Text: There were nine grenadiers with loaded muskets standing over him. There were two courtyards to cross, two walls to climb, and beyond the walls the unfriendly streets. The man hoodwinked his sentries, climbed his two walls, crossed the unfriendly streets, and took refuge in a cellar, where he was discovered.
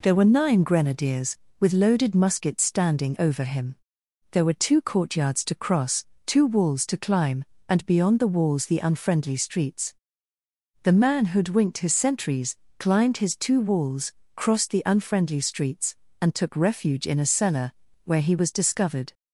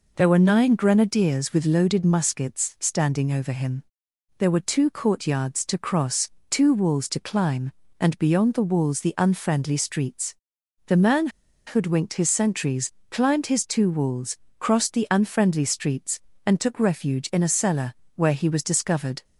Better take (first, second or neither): first